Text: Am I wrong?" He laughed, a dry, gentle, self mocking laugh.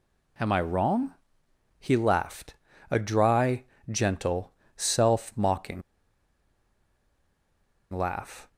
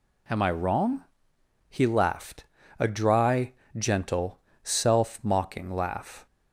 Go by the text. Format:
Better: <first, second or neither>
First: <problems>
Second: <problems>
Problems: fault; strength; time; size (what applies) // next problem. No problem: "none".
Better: second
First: pauses between "mocking" and "laugh"; strong; at 5.8 s; 2.1 s long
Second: none